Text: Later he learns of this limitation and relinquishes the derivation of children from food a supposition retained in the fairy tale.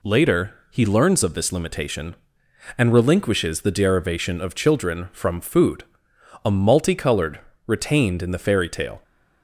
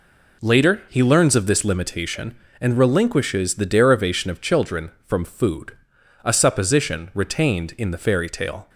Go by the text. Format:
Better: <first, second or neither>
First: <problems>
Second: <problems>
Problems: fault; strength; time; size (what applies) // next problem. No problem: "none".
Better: second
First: pauses between "Later" and "he"; slight; at 0.5 s; 0.16 s long // pauses between "food" and "a"; noticeable; at 5.8 s; 0.60 s long // says "multicolored" for "supposition"; at 6.5 s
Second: pauses between "food" and "a"; noticeable; at 5.7 s; 0.52 s long